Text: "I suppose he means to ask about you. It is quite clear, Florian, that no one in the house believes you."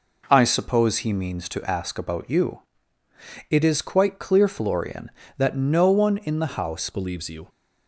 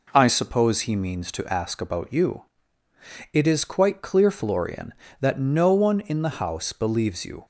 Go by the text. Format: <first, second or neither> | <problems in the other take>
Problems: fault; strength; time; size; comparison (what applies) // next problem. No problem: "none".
second | changes voice at "believes"; from 6.8 s on; 0.6 s long